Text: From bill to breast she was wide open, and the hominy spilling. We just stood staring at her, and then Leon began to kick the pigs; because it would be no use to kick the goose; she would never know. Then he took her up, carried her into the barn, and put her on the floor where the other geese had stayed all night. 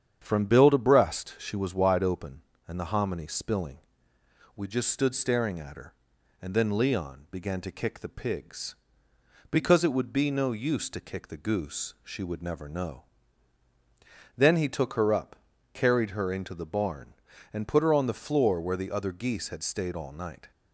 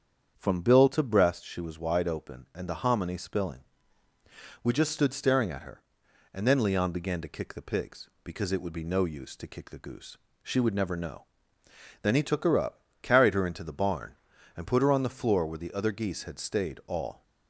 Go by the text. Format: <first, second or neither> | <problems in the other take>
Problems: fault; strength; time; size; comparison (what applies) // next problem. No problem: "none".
first | starts louder than the rest; strong; until 1.3 s; 8 dB; strong in the first // stops before "night"; at 17.2 s